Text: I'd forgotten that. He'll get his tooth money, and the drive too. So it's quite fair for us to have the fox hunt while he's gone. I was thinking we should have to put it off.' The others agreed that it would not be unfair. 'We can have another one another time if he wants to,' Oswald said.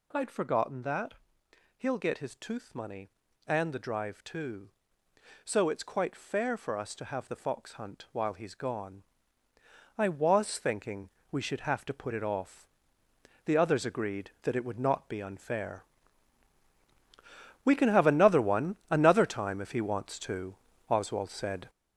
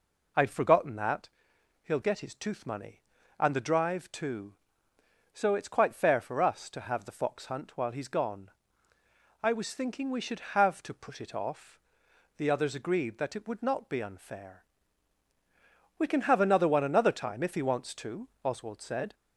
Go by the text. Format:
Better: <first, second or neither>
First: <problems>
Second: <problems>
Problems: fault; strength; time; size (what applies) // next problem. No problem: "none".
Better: second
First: gets louder; strong; throughout; 7.5 dB // pauses between "thinking" and "we"; slight; at 11.0 s; 0.22 s long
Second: none